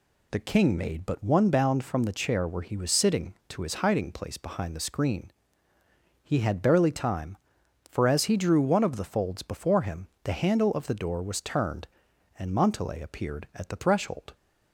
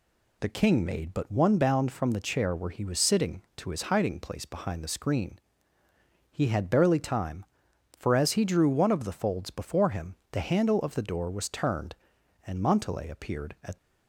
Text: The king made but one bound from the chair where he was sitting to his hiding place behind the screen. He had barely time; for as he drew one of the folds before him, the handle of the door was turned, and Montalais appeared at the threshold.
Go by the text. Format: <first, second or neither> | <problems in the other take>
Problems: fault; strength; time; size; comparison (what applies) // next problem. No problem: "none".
first | stops before "the threshold"; at 13.7 s